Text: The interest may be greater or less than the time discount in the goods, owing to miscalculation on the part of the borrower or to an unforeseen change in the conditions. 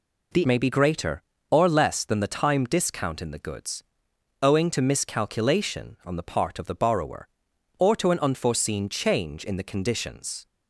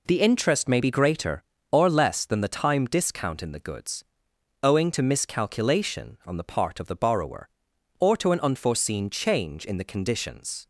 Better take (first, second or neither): second